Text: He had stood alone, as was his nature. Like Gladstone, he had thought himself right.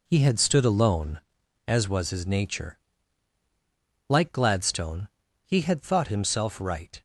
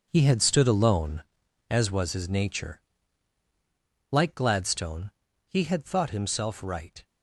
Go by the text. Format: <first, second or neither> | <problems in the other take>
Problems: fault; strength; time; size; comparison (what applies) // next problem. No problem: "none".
first | gets quieter; strong; throughout; 10.5 dB